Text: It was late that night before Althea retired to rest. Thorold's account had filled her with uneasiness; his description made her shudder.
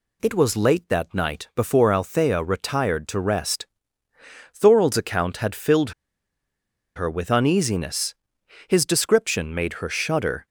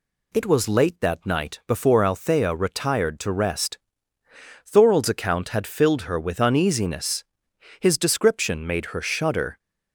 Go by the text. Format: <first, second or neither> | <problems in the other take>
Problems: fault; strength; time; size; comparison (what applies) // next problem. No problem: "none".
second | pauses between "filled" and "her"; at 5.9 s; 1.0 s long